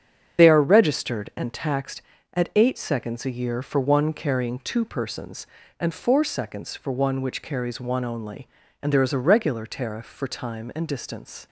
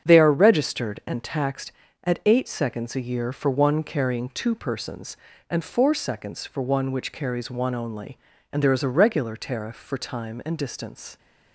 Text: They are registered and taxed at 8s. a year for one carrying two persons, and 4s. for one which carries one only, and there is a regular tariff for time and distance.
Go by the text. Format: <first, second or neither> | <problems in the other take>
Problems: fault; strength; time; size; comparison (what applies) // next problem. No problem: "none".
second | loses the start of "They"; at 0.3 s; 40 ms // starts louder than the rest; strong; until 1.4 s; 7.5 dB; strong in the second